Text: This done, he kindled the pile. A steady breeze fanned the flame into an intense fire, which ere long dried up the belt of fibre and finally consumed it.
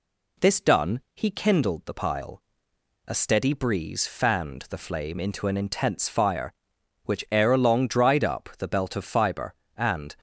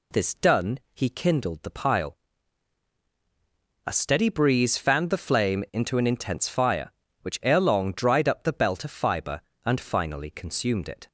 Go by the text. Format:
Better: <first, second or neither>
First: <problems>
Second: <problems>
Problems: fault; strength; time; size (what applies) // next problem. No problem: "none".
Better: second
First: stops before "finally consumed it"; at 10.1 s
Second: none